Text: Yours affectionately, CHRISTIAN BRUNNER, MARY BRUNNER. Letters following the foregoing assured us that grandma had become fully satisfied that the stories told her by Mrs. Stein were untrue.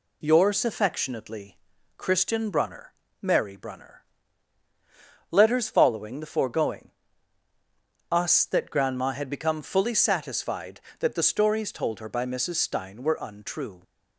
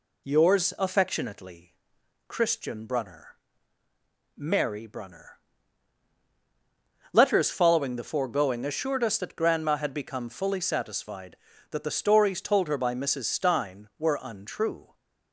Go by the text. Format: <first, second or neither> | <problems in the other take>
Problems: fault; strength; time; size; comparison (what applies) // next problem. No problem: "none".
second | skips "assured"; at 7.5 s